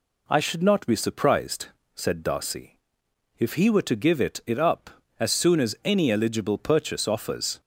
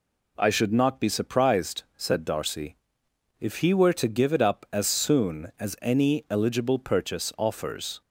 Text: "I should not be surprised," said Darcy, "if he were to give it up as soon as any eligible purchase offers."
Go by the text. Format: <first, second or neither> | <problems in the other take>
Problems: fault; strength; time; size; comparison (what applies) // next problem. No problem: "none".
second | says "it" twice; at 4.4 s